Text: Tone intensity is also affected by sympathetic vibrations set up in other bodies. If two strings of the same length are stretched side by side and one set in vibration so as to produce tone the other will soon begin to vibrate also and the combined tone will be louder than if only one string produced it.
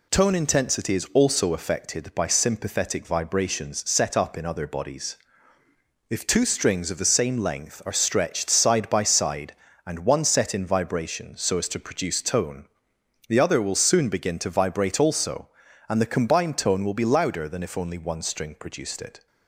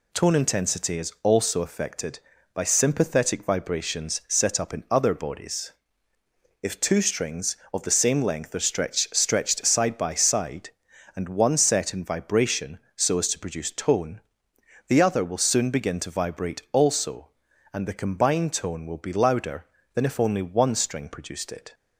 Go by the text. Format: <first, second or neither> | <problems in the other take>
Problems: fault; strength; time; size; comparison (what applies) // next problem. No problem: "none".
first | says "stretched" twice; at 9.1 s // pauses between "tone" and "the"; noticeable; at 14.1 s; 0.68 s long; noticeable in the first